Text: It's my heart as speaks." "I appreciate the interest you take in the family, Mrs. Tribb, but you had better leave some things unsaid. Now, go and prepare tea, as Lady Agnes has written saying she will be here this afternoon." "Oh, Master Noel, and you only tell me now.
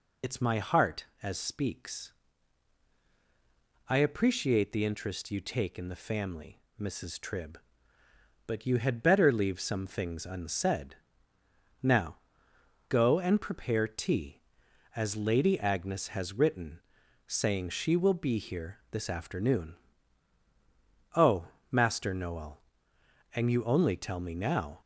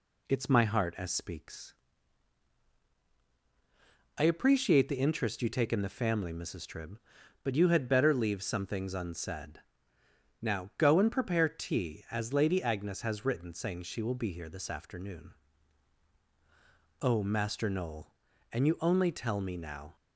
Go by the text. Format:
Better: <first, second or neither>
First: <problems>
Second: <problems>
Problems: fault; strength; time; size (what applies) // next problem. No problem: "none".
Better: second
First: loses the start of "It's"; at 0.2 s; 55 ms // pauses between "written" and "saying"; noticeable; at 16.8 s; 0.46 s long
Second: none